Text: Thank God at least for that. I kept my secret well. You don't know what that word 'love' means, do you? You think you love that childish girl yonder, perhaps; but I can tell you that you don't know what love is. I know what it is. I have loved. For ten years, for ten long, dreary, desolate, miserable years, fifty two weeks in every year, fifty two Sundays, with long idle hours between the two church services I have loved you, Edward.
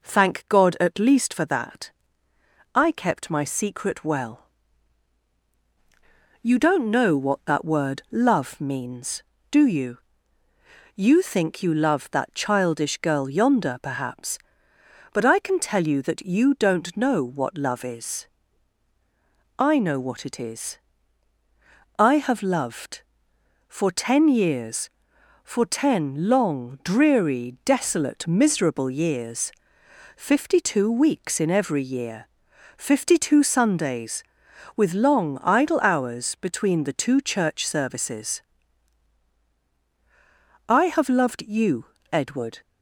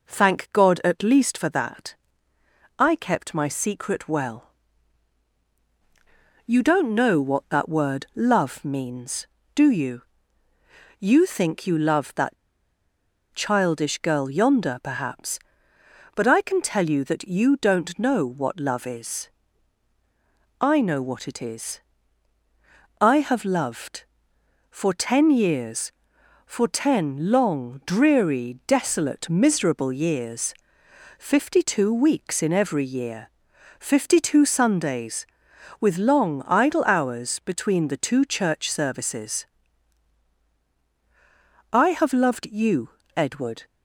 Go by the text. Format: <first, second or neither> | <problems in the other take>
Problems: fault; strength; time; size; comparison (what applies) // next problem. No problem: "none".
first | pauses between "that" and "childish"; at 12.3 s; 0.99 s long // pauses between "services" and "I"; strong; at 39.4 s; 2.2 s long; strong in the first